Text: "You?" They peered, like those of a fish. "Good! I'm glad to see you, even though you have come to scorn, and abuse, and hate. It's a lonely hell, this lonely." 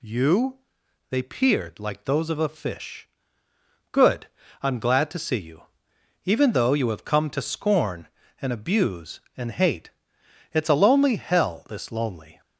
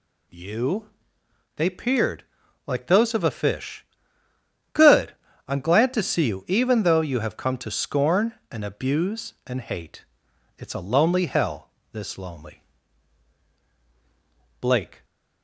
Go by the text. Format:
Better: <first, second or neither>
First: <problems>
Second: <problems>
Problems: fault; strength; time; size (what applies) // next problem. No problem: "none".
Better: first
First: none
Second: goes on to say "Blake"; slight; from 14.6 s on; 0.44 s long